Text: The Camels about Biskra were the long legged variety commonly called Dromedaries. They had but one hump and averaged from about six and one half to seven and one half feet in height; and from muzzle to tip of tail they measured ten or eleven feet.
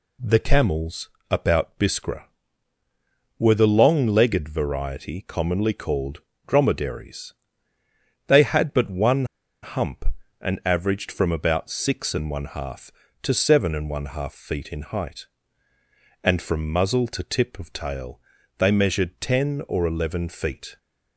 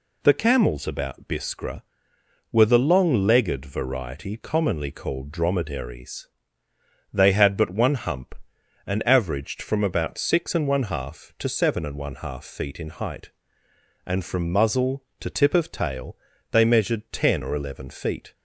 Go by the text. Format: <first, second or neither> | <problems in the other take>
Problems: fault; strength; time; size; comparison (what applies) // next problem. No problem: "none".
second | pauses between "Camels" and "about"; slight; at 1.0 s; 0.22 s long // pauses between "called" and "Dromedaries"; slight; at 6.1 s; 0.26 s long // pauses between "one" and "hump"; at 9.2 s; 0.38 s long // pauses between "tail" and "they"; slight; at 18.2 s; 0.36 s long; slight in the second